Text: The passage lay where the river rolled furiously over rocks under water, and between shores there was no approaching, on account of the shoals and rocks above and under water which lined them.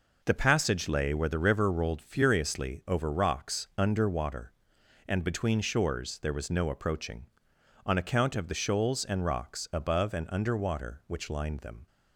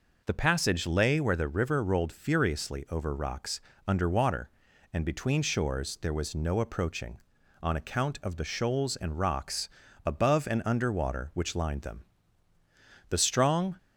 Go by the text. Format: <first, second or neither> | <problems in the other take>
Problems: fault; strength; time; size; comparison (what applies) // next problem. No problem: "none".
first | pauses between "rocks" and "under"; slight; at 3.5 s; 0.26 s long // pauses between "rocks" and "above"; at 9.6 s; 0.38 s long // goes on to say "The strong"; noticeable; from 13.0 s on; 0.68 s long